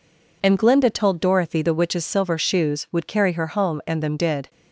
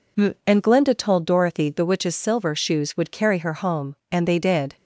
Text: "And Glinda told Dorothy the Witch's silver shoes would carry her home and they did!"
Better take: second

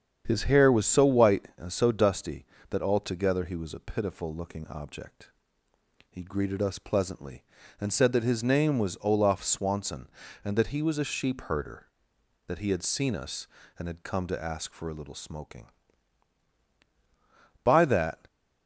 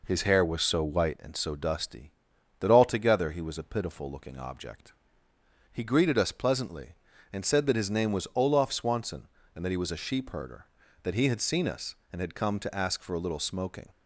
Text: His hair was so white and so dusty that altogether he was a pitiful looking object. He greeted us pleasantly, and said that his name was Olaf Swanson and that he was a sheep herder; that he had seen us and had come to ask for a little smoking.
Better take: second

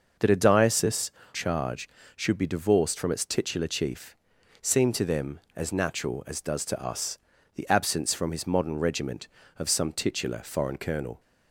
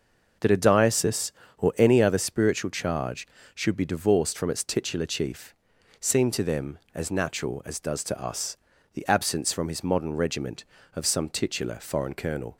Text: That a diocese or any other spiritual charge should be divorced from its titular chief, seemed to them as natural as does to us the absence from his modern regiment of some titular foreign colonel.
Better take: second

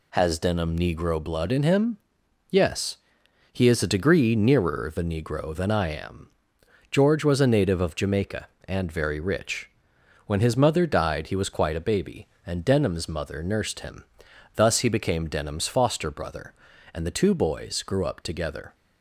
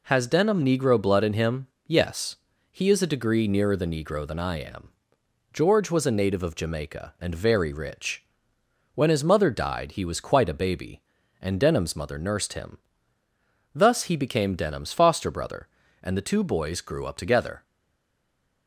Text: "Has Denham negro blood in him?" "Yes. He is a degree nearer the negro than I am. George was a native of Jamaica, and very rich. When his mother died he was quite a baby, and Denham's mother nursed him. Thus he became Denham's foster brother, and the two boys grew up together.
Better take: first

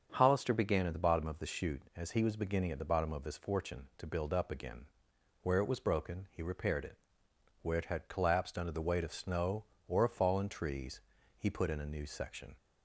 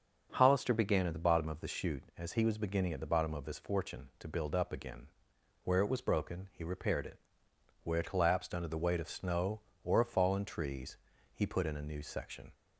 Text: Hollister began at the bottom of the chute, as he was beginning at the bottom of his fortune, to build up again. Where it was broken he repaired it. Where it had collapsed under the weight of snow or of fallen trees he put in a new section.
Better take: first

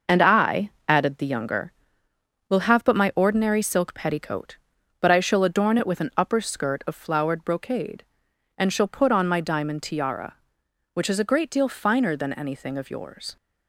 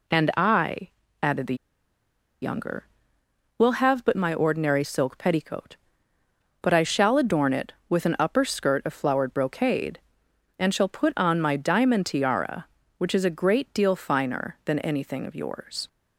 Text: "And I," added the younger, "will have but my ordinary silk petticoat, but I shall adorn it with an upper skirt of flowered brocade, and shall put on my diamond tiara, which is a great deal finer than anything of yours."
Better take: first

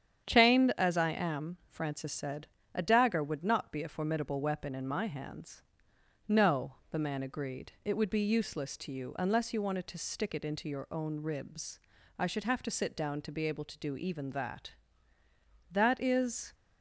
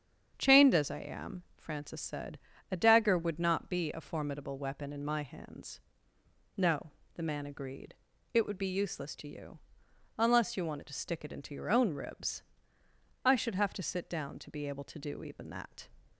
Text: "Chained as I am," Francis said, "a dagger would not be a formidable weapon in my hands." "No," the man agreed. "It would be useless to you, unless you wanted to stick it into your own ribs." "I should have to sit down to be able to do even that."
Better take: second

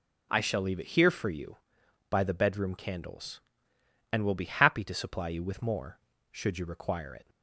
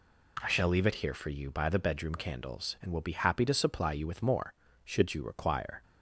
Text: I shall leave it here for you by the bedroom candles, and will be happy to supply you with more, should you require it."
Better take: first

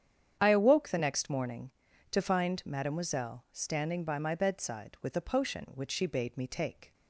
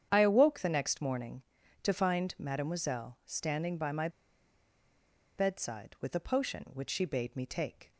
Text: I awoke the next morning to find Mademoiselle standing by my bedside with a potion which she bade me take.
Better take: first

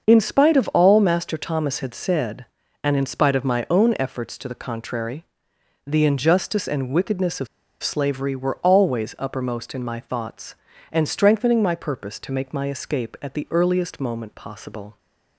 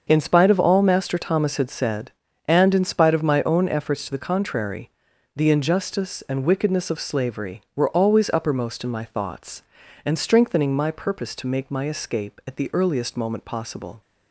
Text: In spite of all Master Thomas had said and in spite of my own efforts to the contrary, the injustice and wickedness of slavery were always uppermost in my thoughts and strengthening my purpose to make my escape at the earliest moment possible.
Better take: second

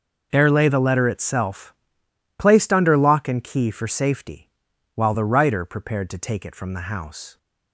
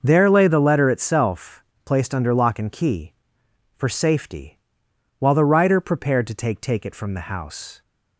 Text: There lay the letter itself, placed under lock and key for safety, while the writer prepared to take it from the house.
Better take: first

